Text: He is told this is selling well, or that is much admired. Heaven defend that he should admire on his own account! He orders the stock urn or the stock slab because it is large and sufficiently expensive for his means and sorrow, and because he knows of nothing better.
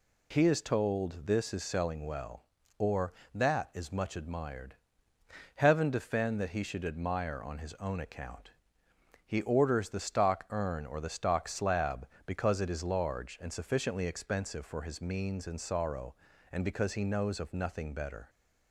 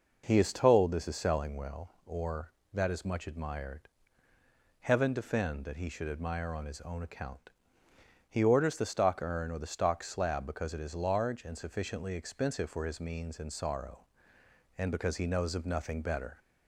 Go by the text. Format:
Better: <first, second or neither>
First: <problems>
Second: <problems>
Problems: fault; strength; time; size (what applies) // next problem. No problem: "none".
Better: neither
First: none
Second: none